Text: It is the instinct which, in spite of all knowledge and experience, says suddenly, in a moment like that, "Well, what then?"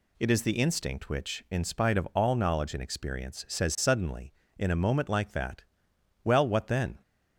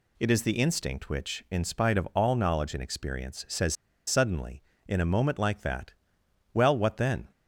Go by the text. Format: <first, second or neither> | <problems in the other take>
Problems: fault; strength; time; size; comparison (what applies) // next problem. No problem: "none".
first | pauses between "says" and "suddenly"; slight; at 3.7 s; 0.32 s long